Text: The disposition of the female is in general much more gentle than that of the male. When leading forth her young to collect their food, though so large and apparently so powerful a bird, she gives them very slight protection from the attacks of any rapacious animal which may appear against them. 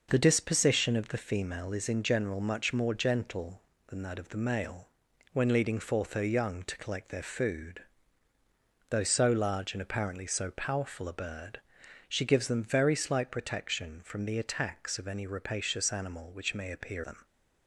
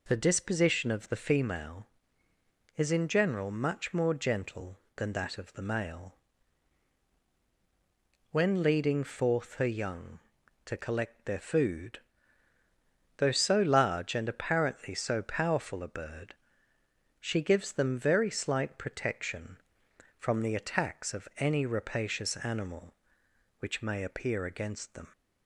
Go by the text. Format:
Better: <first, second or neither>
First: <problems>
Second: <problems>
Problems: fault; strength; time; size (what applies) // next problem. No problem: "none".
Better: second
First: skips "against"; at 17.0 s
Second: none